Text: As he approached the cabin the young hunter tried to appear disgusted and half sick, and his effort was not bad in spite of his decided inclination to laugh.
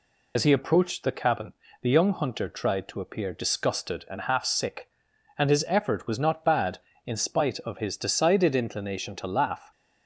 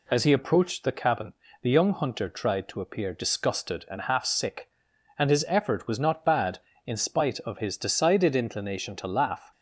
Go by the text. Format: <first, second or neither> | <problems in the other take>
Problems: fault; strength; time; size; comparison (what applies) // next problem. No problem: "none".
second | loses the start of "As"; at 0.3 s; 75 ms // pauses between "cabin" and "the"; slight; at 1.5 s; 0.30 s long; slight in the second